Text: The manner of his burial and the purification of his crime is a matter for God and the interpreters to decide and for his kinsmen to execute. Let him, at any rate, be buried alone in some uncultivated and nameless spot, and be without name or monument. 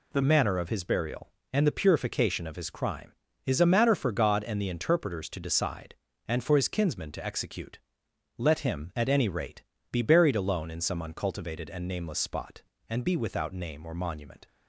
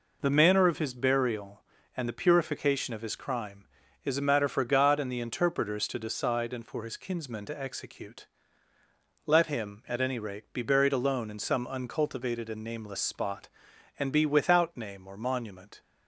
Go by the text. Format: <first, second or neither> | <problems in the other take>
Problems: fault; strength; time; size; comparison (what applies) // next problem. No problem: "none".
second | changes voice at "manner"; from 0.2 s on; 14.2 s long